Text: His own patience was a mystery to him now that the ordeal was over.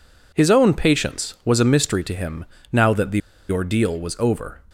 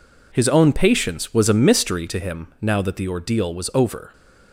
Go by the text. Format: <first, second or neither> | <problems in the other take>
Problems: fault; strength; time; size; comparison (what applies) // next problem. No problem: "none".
second | pauses between "him" and "now"; slight; at 2.4 s; 0.26 s long // pauses between "the" and "ordeal"; slight; at 3.2 s; 0.28 s long